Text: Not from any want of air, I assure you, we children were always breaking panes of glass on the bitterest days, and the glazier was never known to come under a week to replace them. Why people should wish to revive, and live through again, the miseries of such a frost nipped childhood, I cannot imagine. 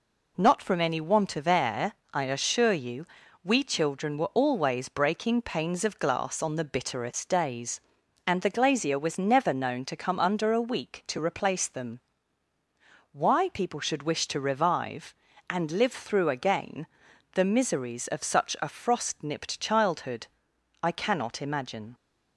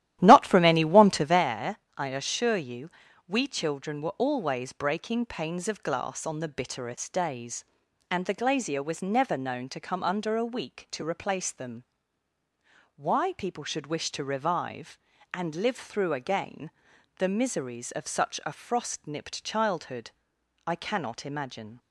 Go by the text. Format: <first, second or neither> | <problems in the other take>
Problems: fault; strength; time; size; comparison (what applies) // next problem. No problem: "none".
first | starts louder than the rest; strong; until 1.5 s; 13 dB